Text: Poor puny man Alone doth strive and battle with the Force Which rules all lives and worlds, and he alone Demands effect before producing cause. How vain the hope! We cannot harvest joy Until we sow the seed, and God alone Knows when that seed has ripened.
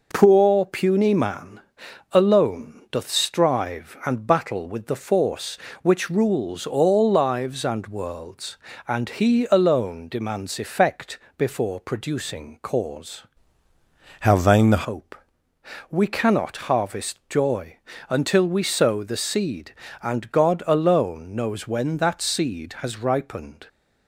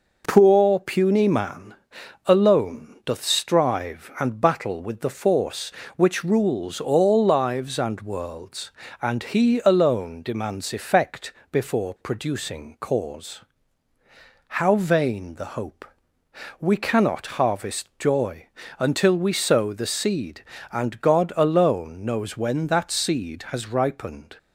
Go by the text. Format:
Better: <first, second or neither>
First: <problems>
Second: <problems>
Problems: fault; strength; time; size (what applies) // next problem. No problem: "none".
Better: second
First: pauses between "man" and "Alone"; noticeable; at 1.6 s; 0.50 s long // pauses between "effect" and "before"; slight; at 11.1 s; 0.20 s long // changes voice from "How" to "the"; from 14.2 to 14.8 s; 0.6 s long // pauses between "joy" and "Until"; slight; at 17.7 s; 0.32 s long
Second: pauses between "man" and "Alone"; noticeable; at 1.7 s; 0.50 s long // pauses between "effect" and "before"; slight; at 11.3 s; 0.20 s long // pauses between "joy" and "Until"; slight; at 18.4 s; 0.32 s long